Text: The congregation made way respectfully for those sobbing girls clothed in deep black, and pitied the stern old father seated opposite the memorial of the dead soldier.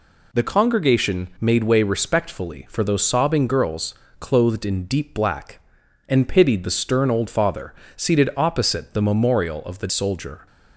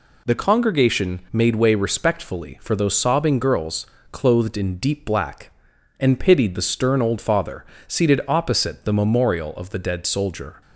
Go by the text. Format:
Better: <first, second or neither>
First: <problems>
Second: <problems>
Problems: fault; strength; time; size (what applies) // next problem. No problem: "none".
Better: second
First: pauses between "girls" and "clothed"; slight; at 3.9 s; 0.26 s long // pauses between "father" and "seated"; slight; at 7.7 s; 0.24 s long // skips "dead"; at 9.8 s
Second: pauses between "girls" and "clothed"; slight; at 3.8 s; 0.26 s long // pauses between "father" and "seated"; slight; at 7.6 s; 0.24 s long